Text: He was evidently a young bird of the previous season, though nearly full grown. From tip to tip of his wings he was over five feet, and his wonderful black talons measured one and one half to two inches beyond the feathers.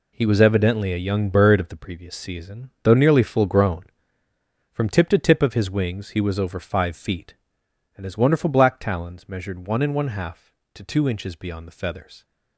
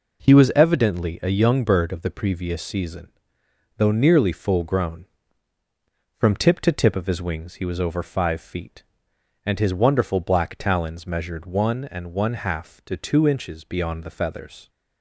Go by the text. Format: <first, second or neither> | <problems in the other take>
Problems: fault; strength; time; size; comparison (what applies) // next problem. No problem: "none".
neither | none